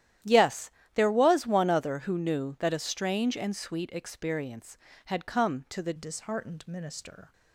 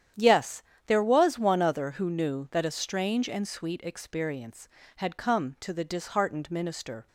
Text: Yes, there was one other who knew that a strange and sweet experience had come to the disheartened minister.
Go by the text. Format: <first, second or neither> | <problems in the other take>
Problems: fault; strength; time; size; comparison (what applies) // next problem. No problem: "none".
second | starts louder than the rest; strong; until 1.5 s; 11.5 dB; strong in the second // changes voice at "disheartened"; from 5.9 s on; 1.4 s long